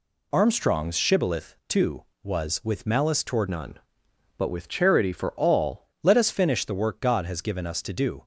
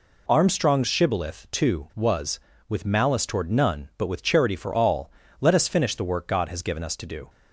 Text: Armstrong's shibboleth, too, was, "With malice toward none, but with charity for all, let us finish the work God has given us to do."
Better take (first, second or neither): second